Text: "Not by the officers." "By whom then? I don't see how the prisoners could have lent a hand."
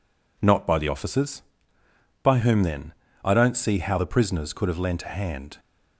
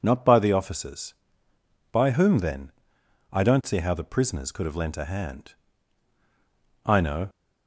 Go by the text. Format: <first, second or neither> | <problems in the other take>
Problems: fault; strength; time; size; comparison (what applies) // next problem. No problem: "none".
first | goes on to say "I know"; slight; from 6.8 s on; 0.44 s long